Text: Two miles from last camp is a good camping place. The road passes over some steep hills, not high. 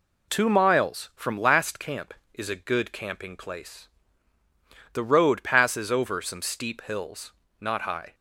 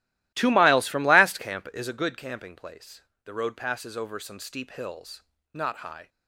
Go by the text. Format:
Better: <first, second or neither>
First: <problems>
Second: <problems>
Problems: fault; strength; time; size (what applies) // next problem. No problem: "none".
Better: first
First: none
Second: starts louder than the rest; strong; until 1.9 s; 15.5 dB